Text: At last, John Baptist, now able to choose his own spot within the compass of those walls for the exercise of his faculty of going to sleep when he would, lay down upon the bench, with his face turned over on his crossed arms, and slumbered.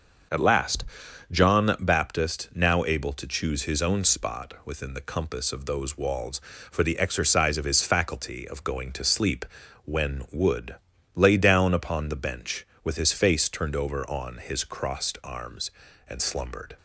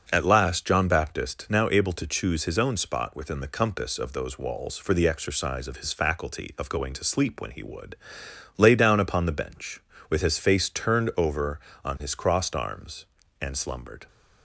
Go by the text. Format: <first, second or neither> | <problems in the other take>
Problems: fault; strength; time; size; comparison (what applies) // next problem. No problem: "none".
second | starts louder than the rest; until 1.8 s; 6.5 dB; also in the second // pauses between "sleep" and "when"; at 9.4 s; 0.40 s long // skips "he"; at 10.2 s